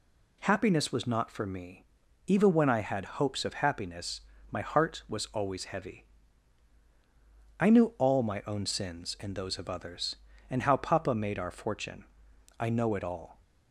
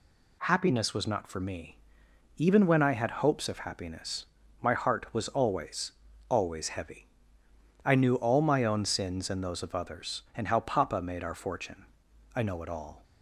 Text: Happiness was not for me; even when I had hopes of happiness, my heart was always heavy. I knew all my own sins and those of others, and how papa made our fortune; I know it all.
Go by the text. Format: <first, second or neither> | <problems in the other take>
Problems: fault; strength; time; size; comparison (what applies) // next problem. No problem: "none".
first | says "always" twice; at 6.2 s